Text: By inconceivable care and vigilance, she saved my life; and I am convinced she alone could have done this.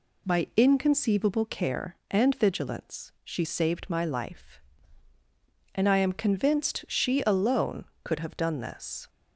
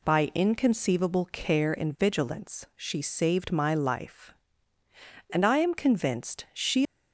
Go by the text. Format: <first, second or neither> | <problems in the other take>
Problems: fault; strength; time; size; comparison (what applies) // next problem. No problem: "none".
first | stops before "alone could have done this"; at 6.8 s